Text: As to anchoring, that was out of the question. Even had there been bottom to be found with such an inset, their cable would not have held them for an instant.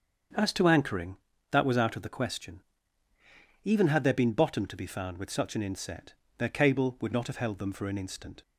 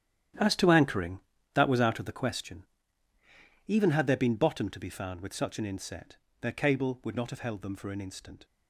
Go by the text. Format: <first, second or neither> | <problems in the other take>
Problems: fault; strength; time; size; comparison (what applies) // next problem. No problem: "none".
first | gets quieter; strong; throughout; 12.5 dB // starts louder than the rest; strong; until 1.6 s; 10.5 dB; also in the first